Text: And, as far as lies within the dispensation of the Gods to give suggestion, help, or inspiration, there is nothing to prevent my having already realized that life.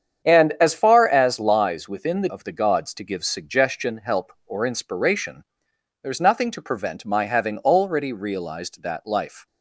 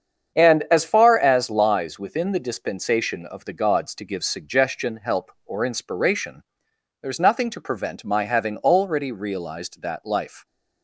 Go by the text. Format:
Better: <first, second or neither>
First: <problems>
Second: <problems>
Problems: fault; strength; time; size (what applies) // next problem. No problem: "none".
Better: second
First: starts louder than the rest; strong; until 1.3 s; 8 dB // skips "dispensation"; at 2.2 s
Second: starts louder than the rest; strong; until 1.4 s; 8 dB